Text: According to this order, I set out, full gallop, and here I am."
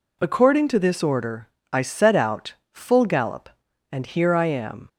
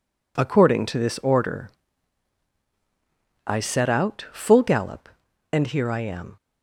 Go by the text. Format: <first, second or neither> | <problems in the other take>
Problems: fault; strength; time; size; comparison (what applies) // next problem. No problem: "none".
neither | none